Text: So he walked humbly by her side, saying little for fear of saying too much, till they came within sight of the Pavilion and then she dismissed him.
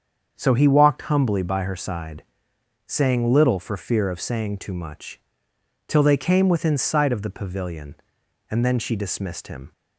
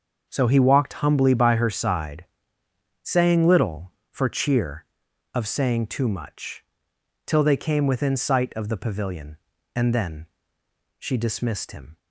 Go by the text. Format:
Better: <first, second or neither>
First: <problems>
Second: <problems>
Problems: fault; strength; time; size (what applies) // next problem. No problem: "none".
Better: first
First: starts louder than the rest; strong; until 1.3 s; 7.5 dB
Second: starts louder than the rest; until 1.3 s; 6.5 dB // says "cheer" for "fear"; at 4.2 s // pauses between "then" and "she"; noticeable; at 10.2 s; 0.72 s long